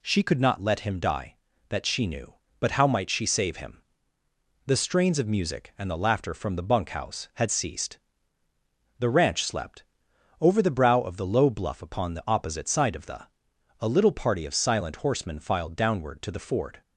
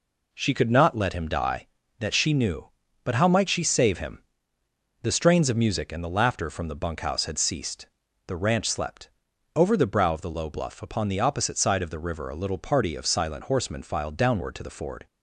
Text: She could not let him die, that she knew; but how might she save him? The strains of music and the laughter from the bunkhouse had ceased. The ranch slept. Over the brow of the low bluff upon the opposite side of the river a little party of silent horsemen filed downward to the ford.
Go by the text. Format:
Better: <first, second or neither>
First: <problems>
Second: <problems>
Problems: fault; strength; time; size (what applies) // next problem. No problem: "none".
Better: second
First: skips "river"; at 13.5 s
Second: none